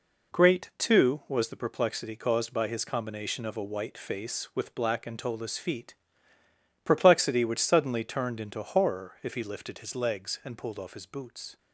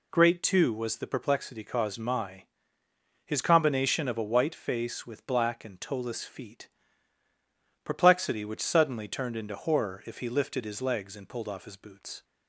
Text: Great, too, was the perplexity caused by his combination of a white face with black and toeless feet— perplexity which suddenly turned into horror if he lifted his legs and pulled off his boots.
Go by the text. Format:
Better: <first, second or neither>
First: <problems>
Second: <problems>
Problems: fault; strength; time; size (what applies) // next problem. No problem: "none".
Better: first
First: none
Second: says "my" for "by"; at 1.9 s